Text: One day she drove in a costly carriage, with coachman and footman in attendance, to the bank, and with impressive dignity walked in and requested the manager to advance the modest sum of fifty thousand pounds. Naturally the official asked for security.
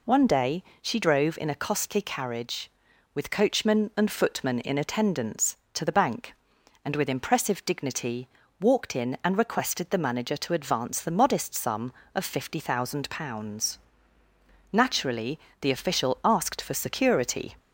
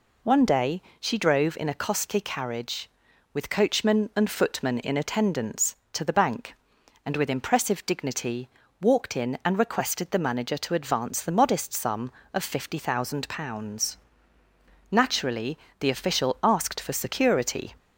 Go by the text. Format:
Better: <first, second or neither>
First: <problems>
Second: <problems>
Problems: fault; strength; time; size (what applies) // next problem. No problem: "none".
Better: neither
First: pauses between "day" and "she"; slight; at 0.6 s; 0.18 s long // pauses between "dignity" and "walked"; slight; at 8.2 s; 0.32 s long // pauses between "Naturally" and "the"; slight; at 15.3 s; 0.22 s long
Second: pauses between "day" and "she"; slight; at 0.8 s; 0.18 s long // pauses between "dignity" and "walked"; slight; at 8.4 s; 0.32 s long // pauses between "Naturally" and "the"; slight; at 15.5 s; 0.22 s long